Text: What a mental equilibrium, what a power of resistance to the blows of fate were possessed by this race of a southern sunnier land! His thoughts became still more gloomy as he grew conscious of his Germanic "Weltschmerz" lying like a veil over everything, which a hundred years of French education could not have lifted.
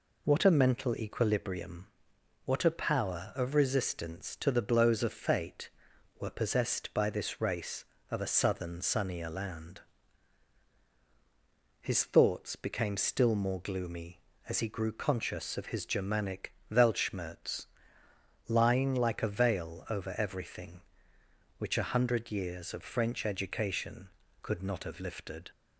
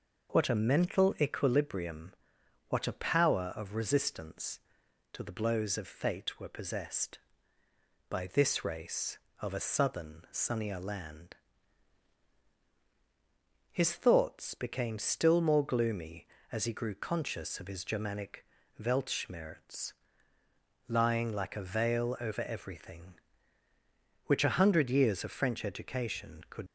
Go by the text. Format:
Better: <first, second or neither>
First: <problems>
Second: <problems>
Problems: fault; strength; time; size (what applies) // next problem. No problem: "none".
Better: first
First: pauses between "Germanic" and "Weltschmerz"; slight; at 16.5 s; 0.18 s long // pauses between "Weltschmerz" and "lying"; noticeable; at 17.6 s; 0.82 s long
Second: pauses between "Germanic" and "Weltschmerz"; slight; at 18.4 s; 0.36 s long // pauses between "Weltschmerz" and "lying"; noticeable; at 19.9 s; 0.92 s long // stops before "not have lifted"; at 26.6 s